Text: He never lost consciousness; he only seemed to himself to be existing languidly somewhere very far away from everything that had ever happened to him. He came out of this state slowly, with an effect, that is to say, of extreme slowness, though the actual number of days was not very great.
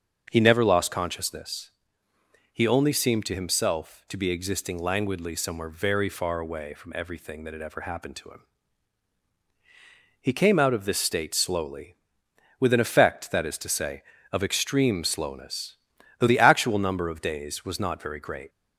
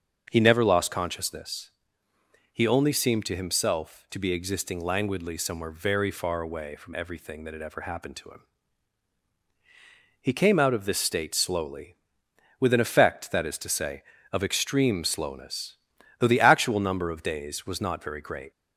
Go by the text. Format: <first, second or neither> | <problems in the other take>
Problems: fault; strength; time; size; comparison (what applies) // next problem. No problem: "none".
neither | starts louder than the rest; the same in both